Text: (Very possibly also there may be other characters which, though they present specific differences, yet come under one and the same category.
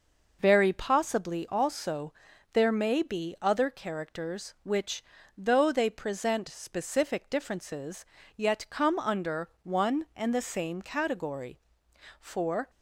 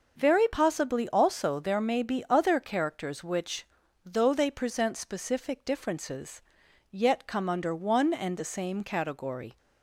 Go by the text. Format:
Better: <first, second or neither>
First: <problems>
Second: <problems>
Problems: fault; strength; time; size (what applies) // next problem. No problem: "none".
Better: second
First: pauses between "also" and "there"; at 2.1 s; 0.40 s long // goes on to say "For"; slight; from 12.2 s on; 0.48 s long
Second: none